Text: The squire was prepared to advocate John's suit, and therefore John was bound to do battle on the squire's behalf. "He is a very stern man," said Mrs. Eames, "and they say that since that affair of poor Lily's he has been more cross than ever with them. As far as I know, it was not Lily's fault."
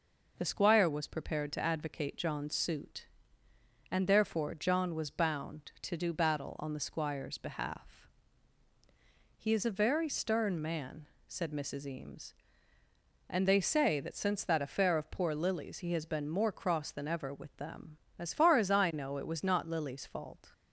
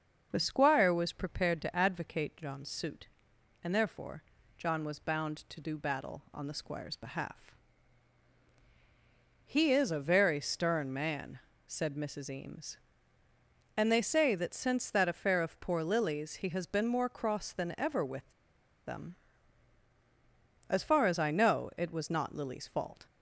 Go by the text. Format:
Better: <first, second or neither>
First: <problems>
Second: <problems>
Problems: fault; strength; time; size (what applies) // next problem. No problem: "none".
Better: first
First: none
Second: starts louder than the rest; noticeable; until 1.3 s; 6 dB // pauses between "therefore" and "John"; slight; at 4.2 s; 0.36 s long // pauses between "with" and "them"; noticeable; at 18.2 s; 0.56 s long